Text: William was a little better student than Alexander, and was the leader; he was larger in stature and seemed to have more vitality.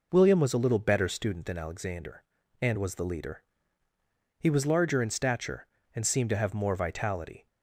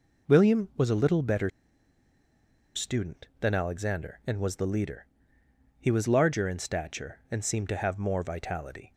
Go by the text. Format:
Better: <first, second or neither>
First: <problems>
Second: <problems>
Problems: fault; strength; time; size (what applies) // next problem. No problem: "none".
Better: first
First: none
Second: pauses between "better" and "student"; strong; at 1.4 s; 1.2 s long